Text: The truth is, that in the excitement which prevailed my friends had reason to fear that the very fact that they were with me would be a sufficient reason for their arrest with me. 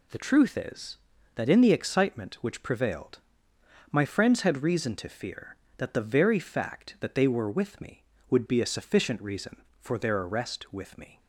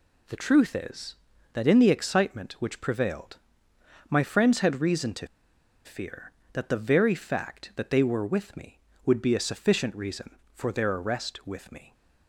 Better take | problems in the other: first | pauses between "prevailed" and "my"; noticeable; at 3.3 s; 0.72 s long; noticeable in the first // pauses between "to" and "fear"; noticeable; at 5.2 s; 0.58 s long

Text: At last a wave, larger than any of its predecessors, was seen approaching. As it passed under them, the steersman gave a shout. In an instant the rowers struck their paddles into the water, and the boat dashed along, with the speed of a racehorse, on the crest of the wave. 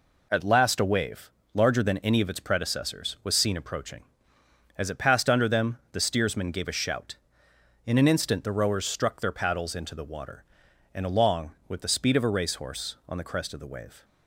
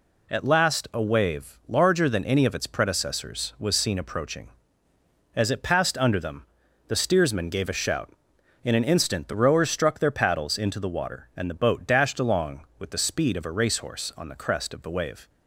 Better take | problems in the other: second | skips "the boat dashed"; at 11.0 s

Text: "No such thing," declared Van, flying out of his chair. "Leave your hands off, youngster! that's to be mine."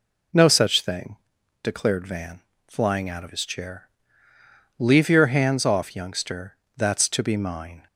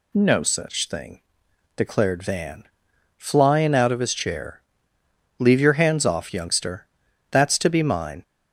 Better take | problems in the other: neither | none

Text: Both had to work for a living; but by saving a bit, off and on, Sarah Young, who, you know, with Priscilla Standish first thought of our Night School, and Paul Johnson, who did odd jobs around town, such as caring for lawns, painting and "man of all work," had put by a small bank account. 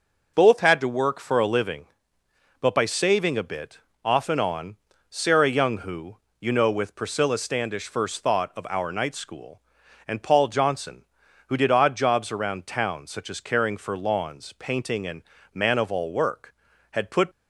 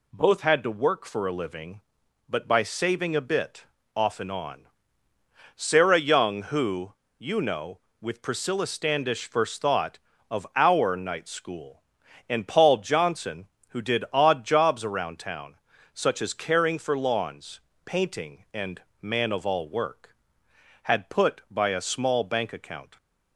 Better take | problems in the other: second | pauses between "and" and "man"; slight; at 15.2 s; 0.30 s long; slight in the second // stops before "by a small bank account"; at 17.3 s

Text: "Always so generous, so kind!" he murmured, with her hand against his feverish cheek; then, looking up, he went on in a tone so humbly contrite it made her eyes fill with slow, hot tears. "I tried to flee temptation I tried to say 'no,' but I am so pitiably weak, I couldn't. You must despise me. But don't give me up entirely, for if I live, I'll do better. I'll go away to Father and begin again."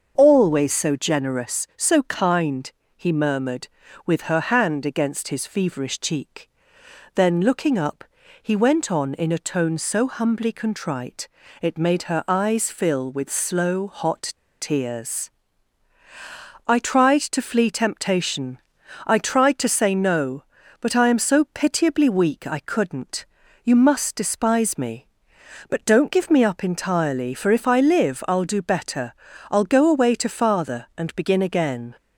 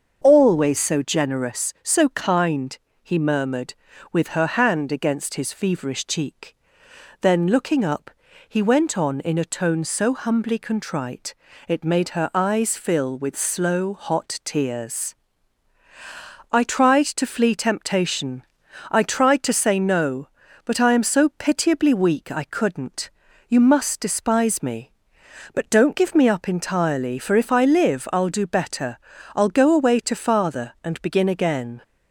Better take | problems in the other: second | starts louder than the rest; until 1.1 s; 6.5 dB; also in the second // pauses between "contrite" and "it"; slight; at 11.2 s; 0.32 s long; slight in the second // pauses between "hot" and "tears"; slight; at 14.3 s; 0.27 s long // pauses between "temptation" and "I"; noticeable; at 18.5 s; 0.48 s long; noticeable in the second

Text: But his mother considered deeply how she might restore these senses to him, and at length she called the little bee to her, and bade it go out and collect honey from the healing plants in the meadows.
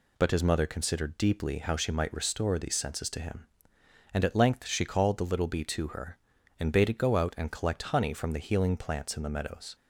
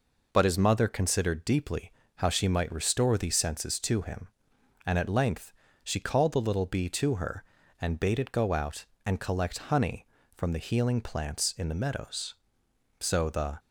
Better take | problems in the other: first | pauses between "deeply" and "how"; slight; at 1.9 s; 0.26 s long // pauses between "length" and "she"; slight; at 5.5 s; 0.30 s long // goes on to say "So the"; from 12.9 s on; 0.60 s long

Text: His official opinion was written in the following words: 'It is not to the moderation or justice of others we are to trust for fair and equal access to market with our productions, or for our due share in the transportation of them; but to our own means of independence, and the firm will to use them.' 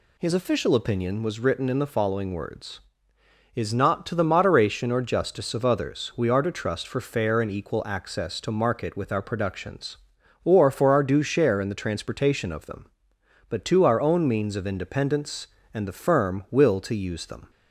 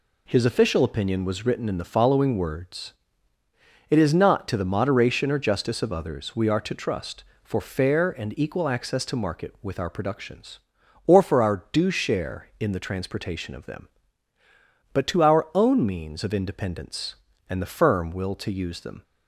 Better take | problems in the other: second | skips "It"; at 3.1 s

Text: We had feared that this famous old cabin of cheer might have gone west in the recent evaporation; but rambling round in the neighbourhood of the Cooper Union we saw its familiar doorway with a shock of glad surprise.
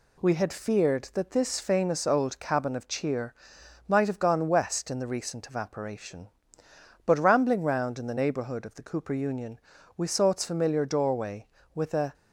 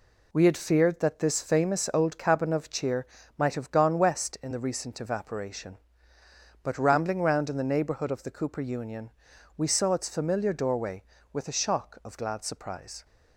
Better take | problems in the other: second | pauses between "cheer" and "might"; noticeable; at 3.3 s; 0.54 s long; slight in the second // pauses between "Union" and "we"; slight; at 9.5 s; 0.36 s long; also in the second // stops before "shock of glad surprise"; at 12.1 s

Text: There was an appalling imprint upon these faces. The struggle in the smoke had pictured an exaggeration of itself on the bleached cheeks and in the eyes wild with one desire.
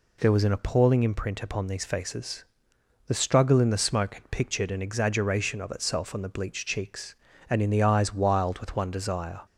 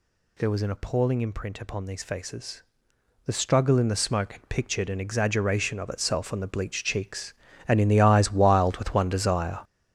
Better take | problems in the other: first | gets louder; strong; throughout; 9.5 dB

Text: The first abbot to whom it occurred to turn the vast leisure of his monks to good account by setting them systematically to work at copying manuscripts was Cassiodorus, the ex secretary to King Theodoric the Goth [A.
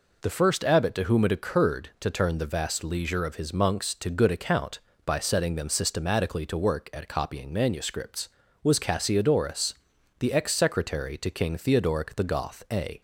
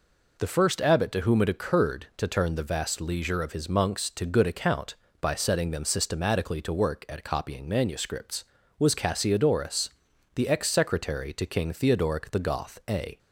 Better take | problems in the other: neither | none

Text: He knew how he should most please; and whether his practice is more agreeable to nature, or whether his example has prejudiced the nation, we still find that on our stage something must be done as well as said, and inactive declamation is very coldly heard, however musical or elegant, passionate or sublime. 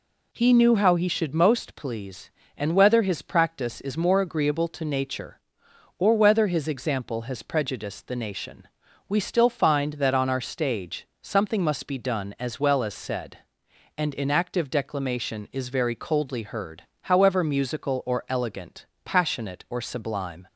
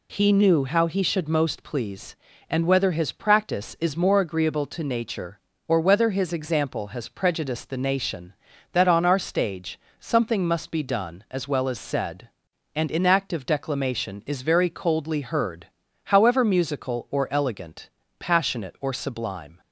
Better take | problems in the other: first | skips "we still find"; at 8.5 s // pauses between "stage" and "something"; slight; at 9.7 s; 0.22 s long; slight in the first

